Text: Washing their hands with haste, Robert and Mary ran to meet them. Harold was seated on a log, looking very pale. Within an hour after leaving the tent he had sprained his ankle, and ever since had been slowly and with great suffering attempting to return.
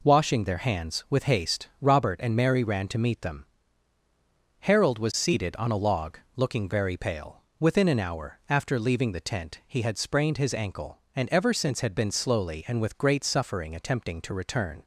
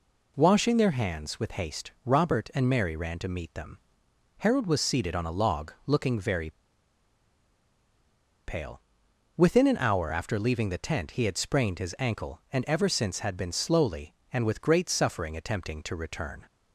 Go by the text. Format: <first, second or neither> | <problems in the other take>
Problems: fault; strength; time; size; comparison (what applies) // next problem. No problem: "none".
first | pauses between "very" and "pale"; strong; at 6.4 s; 1.9 s long